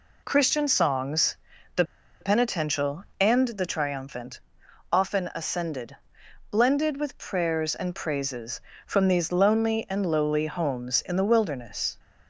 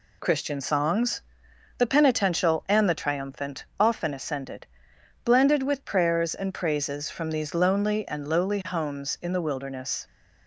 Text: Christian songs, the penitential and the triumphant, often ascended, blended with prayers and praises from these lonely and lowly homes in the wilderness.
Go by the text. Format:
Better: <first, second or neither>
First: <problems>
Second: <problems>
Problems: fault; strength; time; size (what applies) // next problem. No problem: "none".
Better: second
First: pauses between "the" and "penitential"; at 1.8 s; 0.37 s long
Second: none